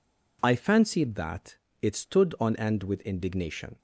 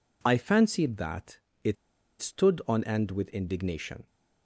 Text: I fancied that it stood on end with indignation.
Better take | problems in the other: first | pauses between "that" and "it"; slight; at 1.3 s; 0.26 s long; slight in the first // pauses between "it" and "stood"; noticeable; at 1.7 s; 0.46 s long

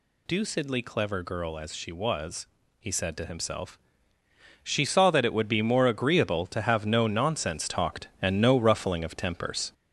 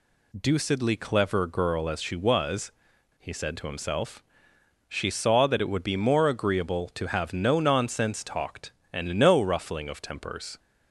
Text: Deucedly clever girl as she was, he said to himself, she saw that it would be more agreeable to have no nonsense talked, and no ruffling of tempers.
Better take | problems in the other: second | gets louder; noticeable; throughout; 5 dB

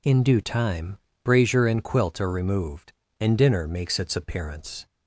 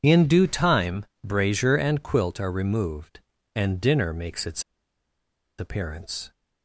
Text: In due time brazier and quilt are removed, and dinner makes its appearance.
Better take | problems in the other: first | pauses between "time" and "brazier"; slight; at 1.0 s; 0.16 s long; slight in the first // pauses between "its" and "appearance"; noticeable; at 4.6 s; 0.95 s long

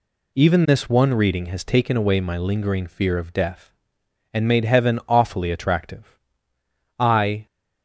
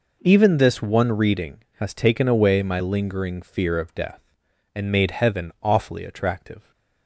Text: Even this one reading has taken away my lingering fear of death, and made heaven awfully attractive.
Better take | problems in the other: second | goes on to say "I"; slight; from 6.9 s on; 0.48 s long

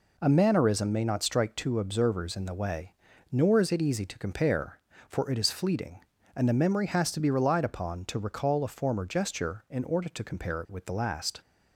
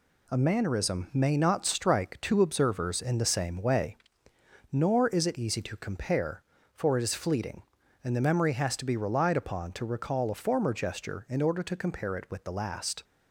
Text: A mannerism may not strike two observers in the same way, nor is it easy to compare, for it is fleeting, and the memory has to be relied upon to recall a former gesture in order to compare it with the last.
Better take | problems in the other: second | skips "same"; at 2.5 s

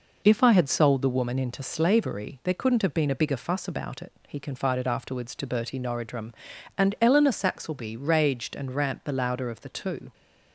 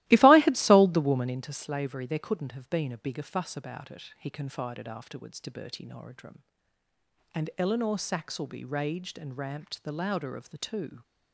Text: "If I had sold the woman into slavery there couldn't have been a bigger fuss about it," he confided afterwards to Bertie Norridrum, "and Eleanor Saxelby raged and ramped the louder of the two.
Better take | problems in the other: first | starts louder than the rest; strong; until 1.4 s; 17 dB

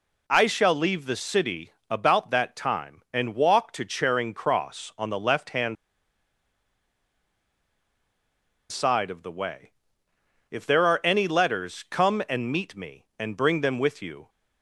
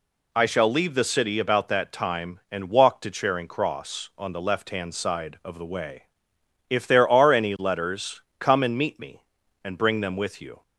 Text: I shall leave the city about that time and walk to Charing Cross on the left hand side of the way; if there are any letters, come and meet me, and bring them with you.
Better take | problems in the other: second | pauses between "city" and "about"; slight; at 1.7 s; 0.18 s long // pauses between "hand" and "side"; strong; at 5.7 s; 2.9 s long

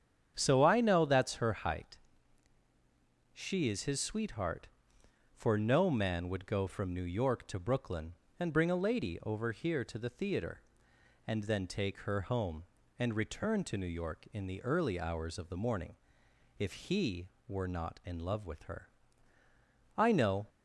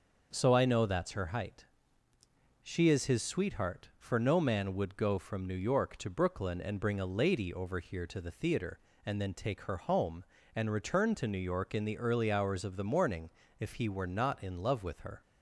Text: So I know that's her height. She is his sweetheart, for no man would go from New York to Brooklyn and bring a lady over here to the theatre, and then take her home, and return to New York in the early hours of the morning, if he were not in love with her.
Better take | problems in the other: second | starts louder than the rest; strong; until 1.3 s; 8 dB; noticeable in the second // goes on to say "I know"; from 19.9 s on; 0.50 s long

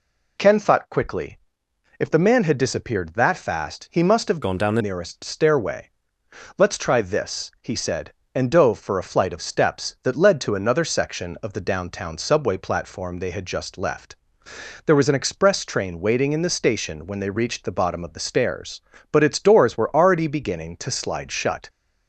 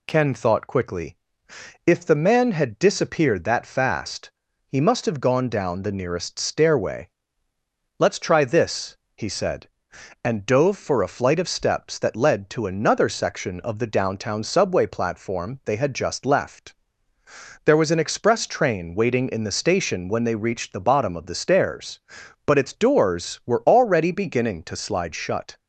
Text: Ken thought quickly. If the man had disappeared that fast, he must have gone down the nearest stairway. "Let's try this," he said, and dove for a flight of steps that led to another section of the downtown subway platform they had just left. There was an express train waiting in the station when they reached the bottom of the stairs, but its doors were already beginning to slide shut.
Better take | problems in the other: second | changes voice from "gone" to "the"; from 4.4 to 4.8 s; 0.4 s long

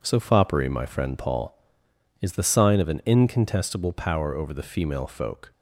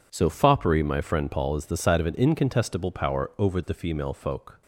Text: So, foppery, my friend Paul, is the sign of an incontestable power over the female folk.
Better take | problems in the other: first | says "side" for "sign"; at 1.7 s

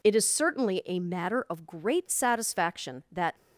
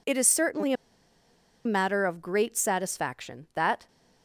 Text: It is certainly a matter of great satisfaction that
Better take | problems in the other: first | pauses between "a" and "matter"; noticeable; at 0.7 s; 0.91 s long

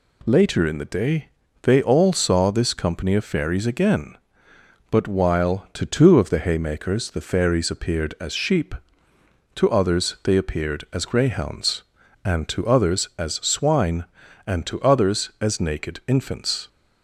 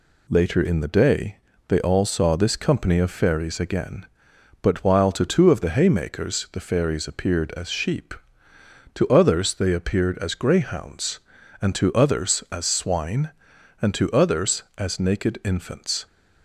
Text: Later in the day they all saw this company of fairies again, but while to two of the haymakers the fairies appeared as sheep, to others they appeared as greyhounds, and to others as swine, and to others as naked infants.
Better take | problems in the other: neither | pauses between "day" and "they"; slight; the same in both

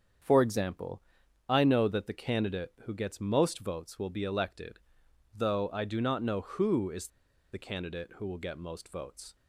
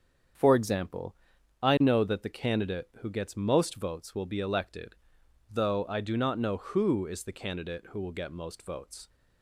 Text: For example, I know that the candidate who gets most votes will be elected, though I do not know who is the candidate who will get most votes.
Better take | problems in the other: second | starts louder than the rest; strong; until 1.6 s; 7.5 dB; strong in the second // pauses between "is" and "the"; at 7.0 s; 0.43 s long

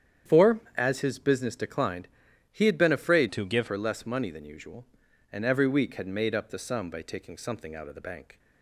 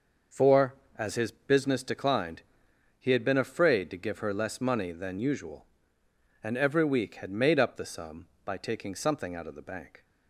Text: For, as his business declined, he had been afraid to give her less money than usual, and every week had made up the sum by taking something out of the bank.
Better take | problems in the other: second | starts louder than the rest; strong; until 1.4 s; 9 dB // changes voice from "to" to "give"; from 3.3 to 3.6 s; 0.3 s long

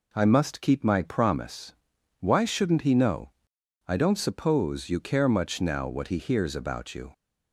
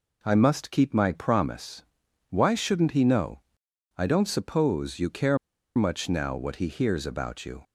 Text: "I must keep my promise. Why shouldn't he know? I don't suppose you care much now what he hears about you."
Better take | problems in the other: first | pauses between "care" and "much"; at 5.3 s; 0.39 s long

